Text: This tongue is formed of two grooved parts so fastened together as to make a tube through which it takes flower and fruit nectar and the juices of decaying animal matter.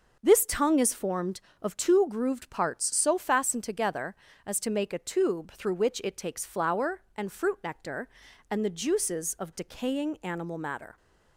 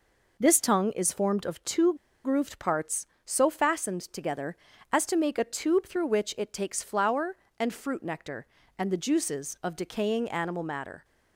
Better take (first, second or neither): first